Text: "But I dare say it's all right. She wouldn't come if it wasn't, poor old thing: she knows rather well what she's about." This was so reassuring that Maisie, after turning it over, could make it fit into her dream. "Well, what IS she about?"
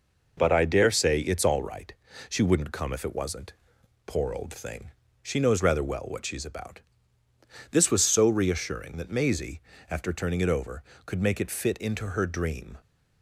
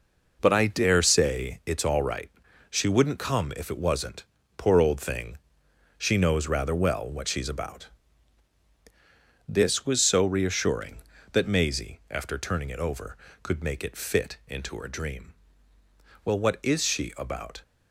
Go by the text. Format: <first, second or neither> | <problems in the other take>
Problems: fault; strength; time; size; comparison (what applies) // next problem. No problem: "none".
second | stops before "Well what IS she about"; at 12.8 s